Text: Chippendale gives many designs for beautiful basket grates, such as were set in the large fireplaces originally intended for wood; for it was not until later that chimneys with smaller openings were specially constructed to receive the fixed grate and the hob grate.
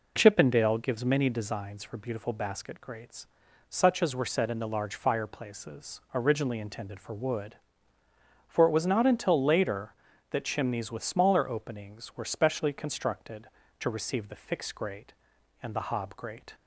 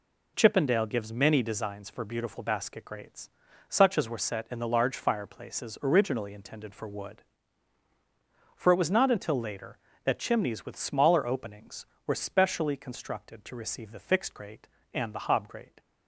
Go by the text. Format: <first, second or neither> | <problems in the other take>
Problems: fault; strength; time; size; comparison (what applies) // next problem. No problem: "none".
neither | none